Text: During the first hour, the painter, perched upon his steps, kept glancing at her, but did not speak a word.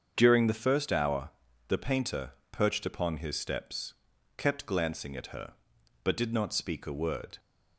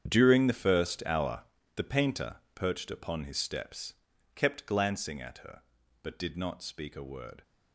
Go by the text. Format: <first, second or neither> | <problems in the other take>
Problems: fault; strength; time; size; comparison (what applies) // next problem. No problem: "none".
first | gets quieter; strong; throughout; 15 dB // starts louder than the rest; strong; until 1.0 s; 8.5 dB; also in the first